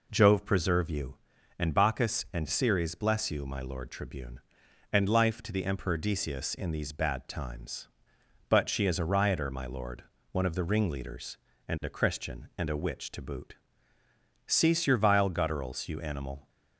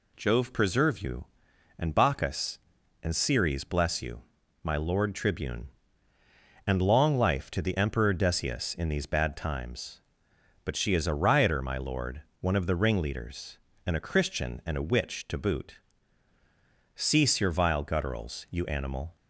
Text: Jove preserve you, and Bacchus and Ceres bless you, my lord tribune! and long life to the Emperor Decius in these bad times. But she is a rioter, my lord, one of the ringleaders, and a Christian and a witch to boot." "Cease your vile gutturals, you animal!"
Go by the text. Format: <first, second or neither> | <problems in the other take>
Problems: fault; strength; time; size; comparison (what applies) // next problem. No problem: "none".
second | skips "long"; at 5.0 s